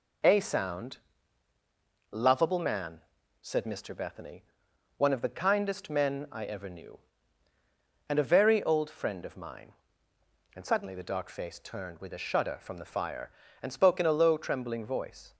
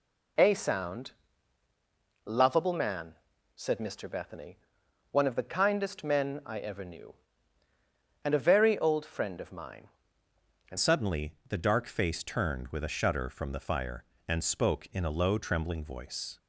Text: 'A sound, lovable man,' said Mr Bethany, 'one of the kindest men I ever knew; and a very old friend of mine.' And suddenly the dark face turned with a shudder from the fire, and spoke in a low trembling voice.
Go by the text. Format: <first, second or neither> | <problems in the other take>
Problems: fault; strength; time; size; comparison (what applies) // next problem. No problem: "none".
first | changes voice at "suddenly"; from 10.7 s on; 5.6 s long